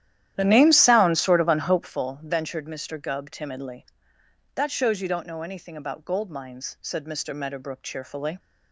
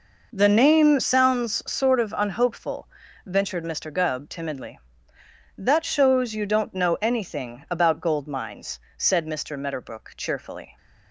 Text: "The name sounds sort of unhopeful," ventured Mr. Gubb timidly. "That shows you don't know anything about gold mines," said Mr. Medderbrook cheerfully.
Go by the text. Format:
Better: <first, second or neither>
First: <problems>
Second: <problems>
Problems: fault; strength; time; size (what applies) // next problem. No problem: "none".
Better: second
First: starts louder than the rest; strong; until 1.9 s; 12 dB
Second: none